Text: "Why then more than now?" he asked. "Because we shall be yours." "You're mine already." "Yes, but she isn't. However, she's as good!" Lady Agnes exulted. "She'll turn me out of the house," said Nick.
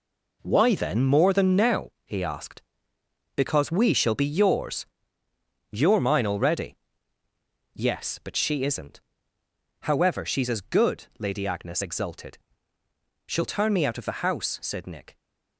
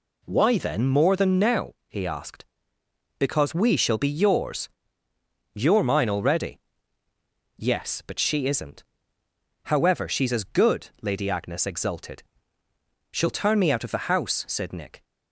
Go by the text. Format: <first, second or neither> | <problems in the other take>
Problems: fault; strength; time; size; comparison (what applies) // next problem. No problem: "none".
second | gets quieter; strong; throughout; 9 dB